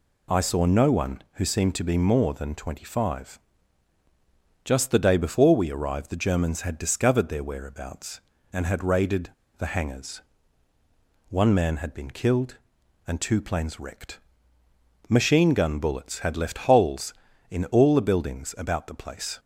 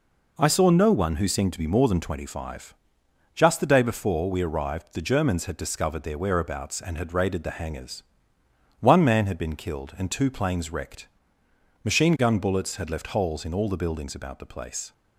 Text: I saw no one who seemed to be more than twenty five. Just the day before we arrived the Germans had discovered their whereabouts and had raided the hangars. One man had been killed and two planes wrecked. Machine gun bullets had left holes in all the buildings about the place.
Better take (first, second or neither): second